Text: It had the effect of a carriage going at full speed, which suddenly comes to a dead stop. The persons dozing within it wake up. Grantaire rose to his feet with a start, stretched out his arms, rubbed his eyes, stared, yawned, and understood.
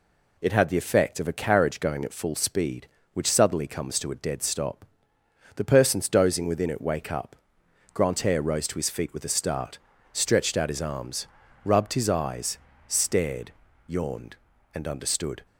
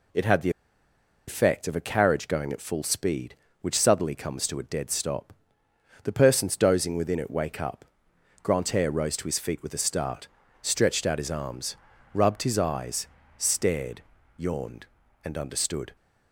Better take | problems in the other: first | pauses between "the" and "effect"; noticeable; at 0.4 s; 0.77 s long

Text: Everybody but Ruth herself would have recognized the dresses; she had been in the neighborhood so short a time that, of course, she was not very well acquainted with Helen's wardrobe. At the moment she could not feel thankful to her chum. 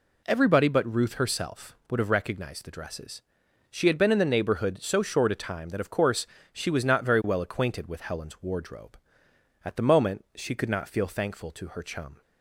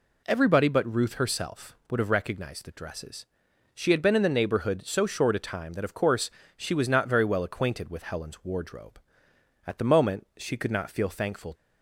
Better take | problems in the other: first | stops before "to her chum"; at 11.5 s

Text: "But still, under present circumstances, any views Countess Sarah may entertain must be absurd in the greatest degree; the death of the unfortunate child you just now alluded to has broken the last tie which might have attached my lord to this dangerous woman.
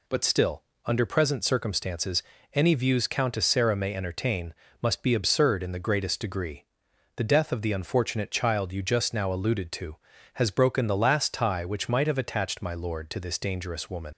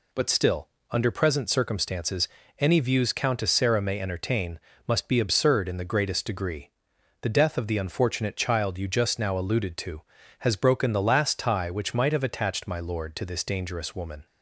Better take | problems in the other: second | pauses between "entertain" and "must"; slight; at 4.5 s; 0.26 s long; slight in the second // leaves "woman" unfinished; at 14.1 s; 70 ms

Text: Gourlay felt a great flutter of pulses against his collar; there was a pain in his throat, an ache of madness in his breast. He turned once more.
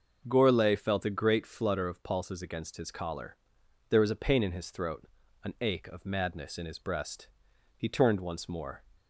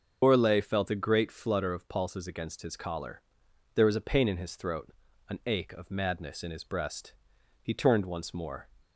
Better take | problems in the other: first | loses the start of "Gourlay"; at 0.2 s; 130 ms // starts louder than the rest; until 1.2 s; 6 dB; also in the first

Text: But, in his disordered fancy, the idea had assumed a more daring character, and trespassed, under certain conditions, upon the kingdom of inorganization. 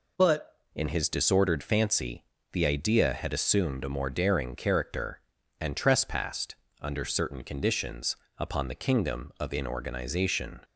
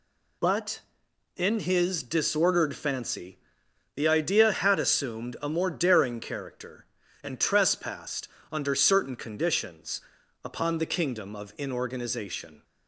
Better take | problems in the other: second | changes voice at "in"; from 0.7 s on; 9.9 s long

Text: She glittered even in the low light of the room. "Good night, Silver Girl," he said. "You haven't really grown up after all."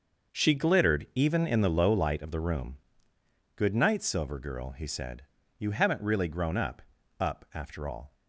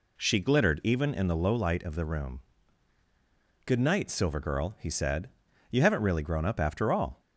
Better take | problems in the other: second | starts louder than the rest; until 1.4 s; 6.5 dB // says "up" twice; at 7.1 s

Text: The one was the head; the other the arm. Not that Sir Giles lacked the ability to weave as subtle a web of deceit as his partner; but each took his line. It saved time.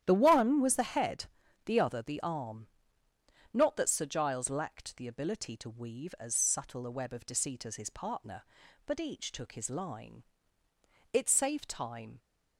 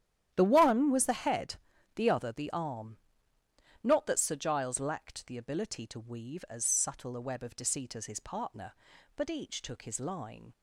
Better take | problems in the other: first | starts louder than the rest; strong; until 1.3 s; 11 dB; strong in the first // stops before "It saved time"; at 10.5 s

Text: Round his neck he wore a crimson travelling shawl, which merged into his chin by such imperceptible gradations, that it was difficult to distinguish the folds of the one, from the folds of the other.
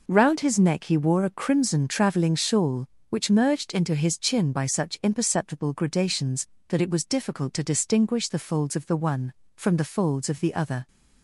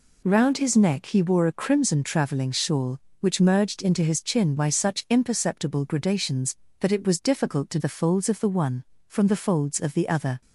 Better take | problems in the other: first | skips "distinguish"; at 7.7 s

